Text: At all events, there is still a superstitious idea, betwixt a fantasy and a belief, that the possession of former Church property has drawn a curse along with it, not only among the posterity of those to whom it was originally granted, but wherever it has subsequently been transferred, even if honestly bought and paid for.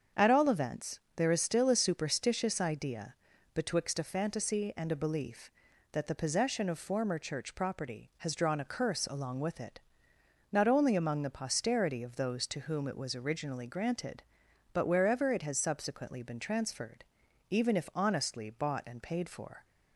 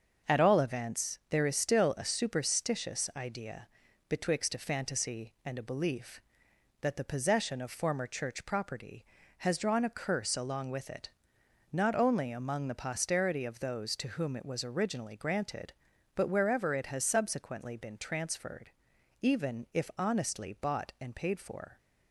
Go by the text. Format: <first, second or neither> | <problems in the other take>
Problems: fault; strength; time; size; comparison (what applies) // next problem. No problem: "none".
neither | starts louder than the rest; the same in both